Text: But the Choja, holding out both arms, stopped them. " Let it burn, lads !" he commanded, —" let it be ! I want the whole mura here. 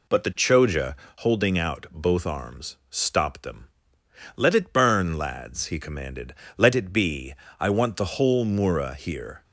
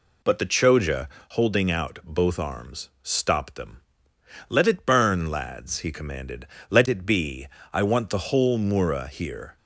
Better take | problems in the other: neither | none

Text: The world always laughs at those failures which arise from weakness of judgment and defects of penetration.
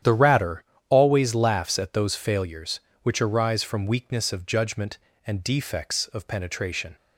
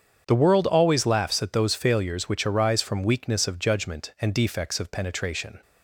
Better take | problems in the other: second | starts louder than the rest; strong; until 1.2 s; 10 dB; strong in the second // says "ratter" for "world"; at 0.1 s

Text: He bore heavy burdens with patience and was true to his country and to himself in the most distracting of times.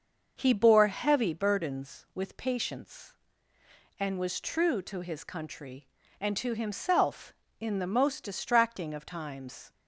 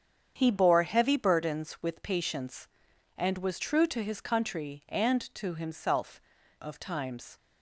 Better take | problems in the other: first | starts louder than the rest; strong; until 1.3 s; 8 dB; also in the first // skips "in the most distracting"; at 6.4 s

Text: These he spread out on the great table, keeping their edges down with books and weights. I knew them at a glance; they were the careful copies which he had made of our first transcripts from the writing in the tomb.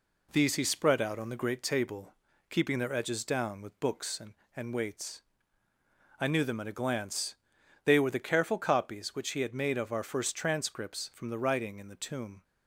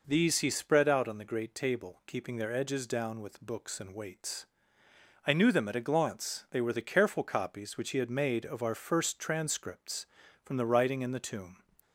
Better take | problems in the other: second | says "and" twice; at 4.5 s

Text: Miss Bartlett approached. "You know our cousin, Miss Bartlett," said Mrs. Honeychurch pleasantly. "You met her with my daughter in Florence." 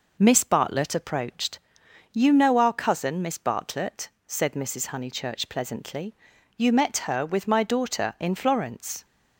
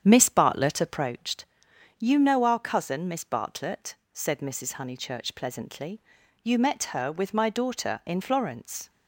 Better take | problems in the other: first | starts louder than the rest; strong; until 1.2 s; 8.5 dB

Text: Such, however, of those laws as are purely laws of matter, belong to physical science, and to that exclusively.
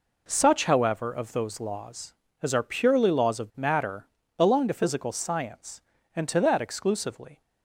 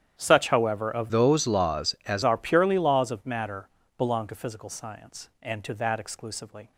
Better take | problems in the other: first | starts louder than the rest; strong; until 1.1 s; 10 dB // changes voice from "those" to "as"; from 1.1 to 2.2 s; 1.1 s long

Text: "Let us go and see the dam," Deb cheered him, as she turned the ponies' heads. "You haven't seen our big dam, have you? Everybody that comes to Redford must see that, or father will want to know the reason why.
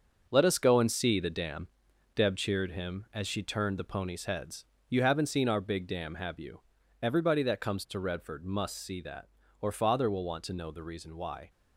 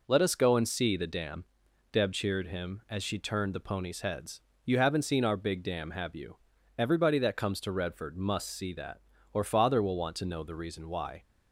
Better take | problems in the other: second | gets quieter; strong; throughout; 7.5 dB

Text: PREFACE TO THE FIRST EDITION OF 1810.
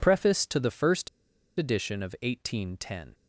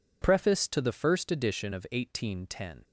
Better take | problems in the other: second | pauses between "FIRST" and "EDITION"; noticeable; at 1.0 s; 0.51 s long

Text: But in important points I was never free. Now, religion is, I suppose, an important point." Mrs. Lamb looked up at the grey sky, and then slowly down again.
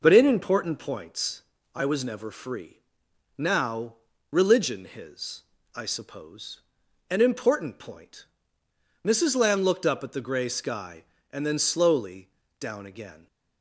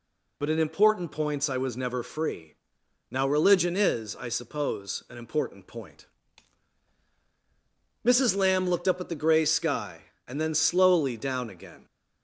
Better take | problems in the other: second | pauses between "points" and "I"; slight; at 1.4 s; 0.34 s long // says "his" for "is"; at 4.8 s // pauses between "slowly" and "down"; slight; at 12.2 s; 0.32 s long

